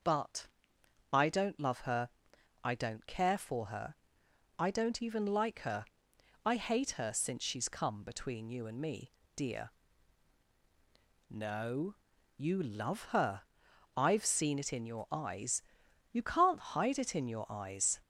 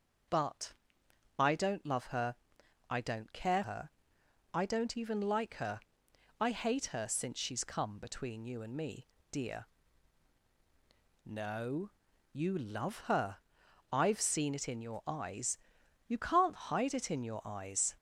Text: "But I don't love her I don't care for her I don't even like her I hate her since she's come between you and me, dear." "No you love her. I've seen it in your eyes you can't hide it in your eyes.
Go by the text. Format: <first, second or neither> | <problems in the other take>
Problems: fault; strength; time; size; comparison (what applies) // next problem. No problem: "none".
first | starts louder than the rest; until 1.9 s; 6 dB; also in the first // pauses between "But" and "I"; noticeable; at 0.7 s; 0.64 s long; noticeable in the first // pauses between "her" and "I"; noticeable; at 2.3 s; 0.54 s long; noticeable in the first // skips "for"; at 3.6 s // pauses between "her" and "I"; noticeable; at 3.8 s; 0.64 s long; noticeable in the first // pauses between "her" and "I"; noticeable; at 5.8 s; 0.58 s long; noticeable in the first // pauses between "No" and "you"; at 11.8 s; 0.42 s long; also in the first // pauses between "eyes" and "you"; noticeable; at 15.5 s; 0.50 s long; noticeable in the first